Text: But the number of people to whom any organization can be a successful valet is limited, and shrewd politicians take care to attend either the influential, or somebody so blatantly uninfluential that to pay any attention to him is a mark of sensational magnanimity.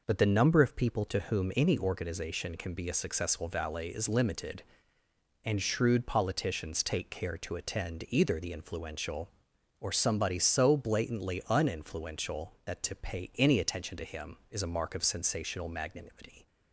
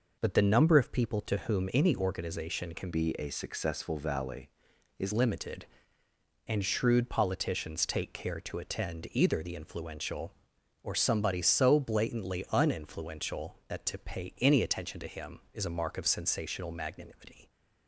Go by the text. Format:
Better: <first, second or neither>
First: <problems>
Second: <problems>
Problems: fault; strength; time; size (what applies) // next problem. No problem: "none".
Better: first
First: none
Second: changes voice from "be" to "is"; from 2.9 to 5.1 s; 2.2 s long